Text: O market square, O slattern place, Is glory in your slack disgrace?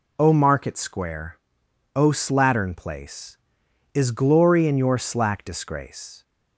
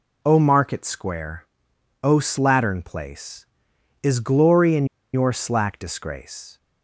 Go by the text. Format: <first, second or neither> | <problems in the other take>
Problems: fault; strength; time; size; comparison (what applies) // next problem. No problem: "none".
first | pauses between "in" and "your"; slight; at 4.8 s; 0.28 s long